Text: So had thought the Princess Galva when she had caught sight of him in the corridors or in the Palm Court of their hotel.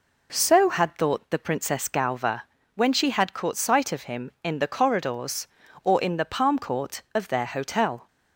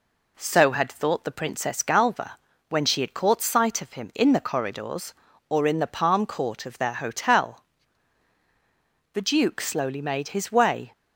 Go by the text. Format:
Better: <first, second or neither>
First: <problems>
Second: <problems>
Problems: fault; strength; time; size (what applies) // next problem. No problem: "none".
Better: first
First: pauses between "Galva" and "when"; slight; at 2.4 s; 0.32 s long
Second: pauses between "Galva" and "when"; slight; at 2.3 s; 0.30 s long // goes on to say "The duke slowly made his way"; strong; from 9.1 s on; 1.7 s long